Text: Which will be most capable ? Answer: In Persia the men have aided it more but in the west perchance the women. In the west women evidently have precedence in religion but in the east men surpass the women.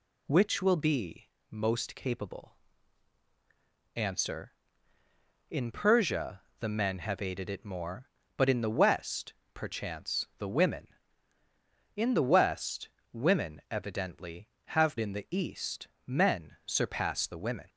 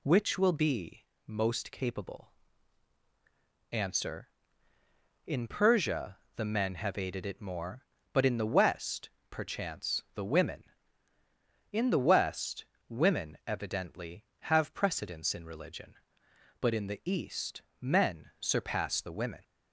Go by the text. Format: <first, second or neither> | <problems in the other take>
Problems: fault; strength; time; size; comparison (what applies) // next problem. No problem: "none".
second | pauses between "be" and "most"; slight; at 1.2 s; 0.24 s long; slight in the second // pauses between "Persia" and "the"; slight; at 6.4 s; 0.18 s long; slight in the second // pauses between "west" and "perchance"; slight; at 9.3 s; 0.20 s long; slight in the second // pauses between "west" and "women"; slight; at 12.8 s; 0.24 s long; slight in the second // skips "precedence in religion but"; at 14.9 s // pauses between "east" and "men"; slight; at 15.8 s; 0.18 s long; slight in the second